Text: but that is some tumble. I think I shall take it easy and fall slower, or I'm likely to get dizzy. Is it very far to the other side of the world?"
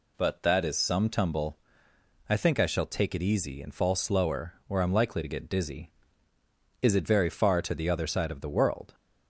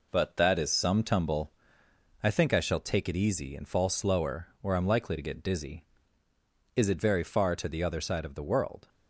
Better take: first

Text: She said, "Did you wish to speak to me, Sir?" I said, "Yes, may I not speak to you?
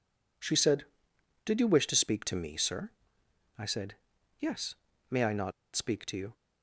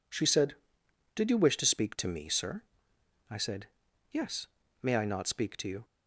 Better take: second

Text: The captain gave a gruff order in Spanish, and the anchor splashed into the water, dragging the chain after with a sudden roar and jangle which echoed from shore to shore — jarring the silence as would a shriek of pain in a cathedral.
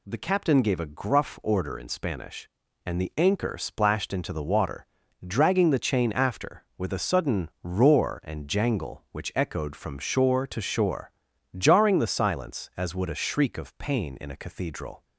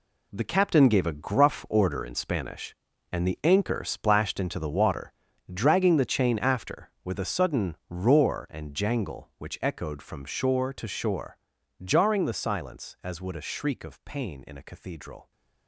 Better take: first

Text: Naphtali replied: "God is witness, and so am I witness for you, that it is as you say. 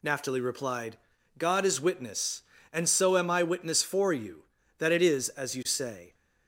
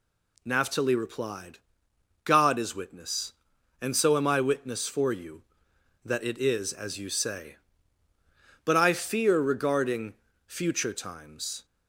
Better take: first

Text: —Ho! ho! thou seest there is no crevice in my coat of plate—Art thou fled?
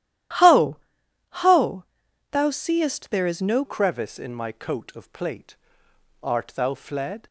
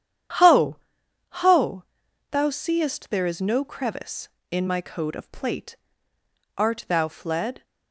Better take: second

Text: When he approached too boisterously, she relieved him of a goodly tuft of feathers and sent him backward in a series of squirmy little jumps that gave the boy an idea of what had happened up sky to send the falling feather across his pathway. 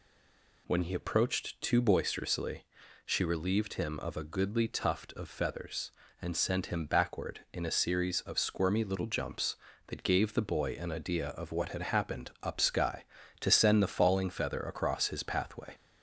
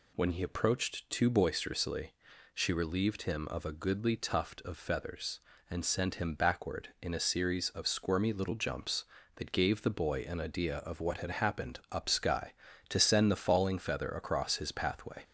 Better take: second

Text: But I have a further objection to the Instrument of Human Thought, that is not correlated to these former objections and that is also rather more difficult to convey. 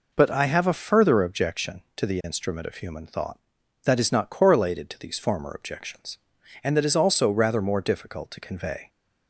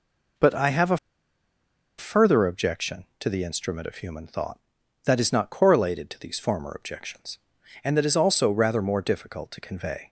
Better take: first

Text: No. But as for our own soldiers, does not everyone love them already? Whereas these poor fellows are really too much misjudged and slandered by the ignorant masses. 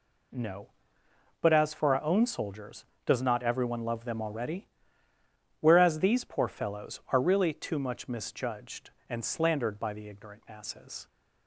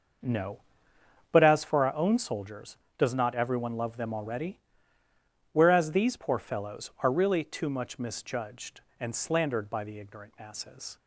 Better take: first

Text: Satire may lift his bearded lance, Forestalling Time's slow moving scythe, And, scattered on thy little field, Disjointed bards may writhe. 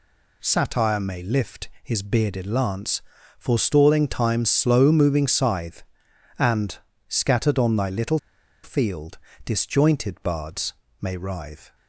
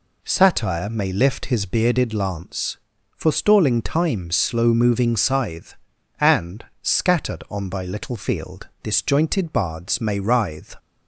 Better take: second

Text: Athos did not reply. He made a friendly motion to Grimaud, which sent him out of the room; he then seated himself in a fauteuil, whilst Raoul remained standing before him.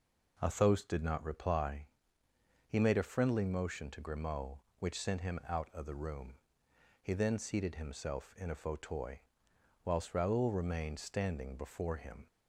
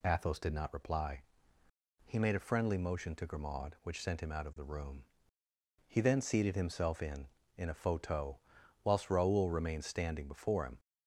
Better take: first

